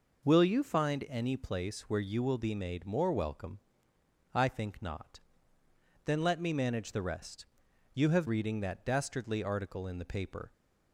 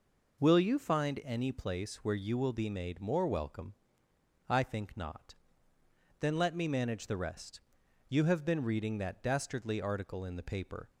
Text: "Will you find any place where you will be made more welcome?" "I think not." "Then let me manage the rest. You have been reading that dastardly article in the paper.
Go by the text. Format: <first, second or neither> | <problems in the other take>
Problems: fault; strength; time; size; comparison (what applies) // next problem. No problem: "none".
second | skips "been"; at 8.2 s